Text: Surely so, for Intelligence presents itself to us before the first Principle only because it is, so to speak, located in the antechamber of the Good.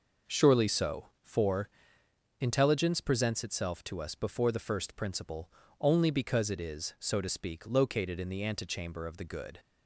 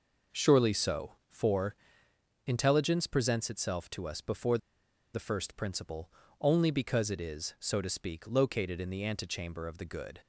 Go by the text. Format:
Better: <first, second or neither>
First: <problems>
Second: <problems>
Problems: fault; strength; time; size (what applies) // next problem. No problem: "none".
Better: first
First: pauses between "for" and "Intelligence"; noticeable; at 1.6 s; 0.72 s long // pauses between "Principle" and "only"; slight; at 5.5 s; 0.30 s long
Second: pauses between "for" and "Intelligence"; noticeable; at 1.7 s; 0.72 s long // pauses between "before" and "the"; noticeable; at 4.5 s; 0.55 s long // pauses between "Principle" and "only"; slight; at 6.1 s; 0.30 s long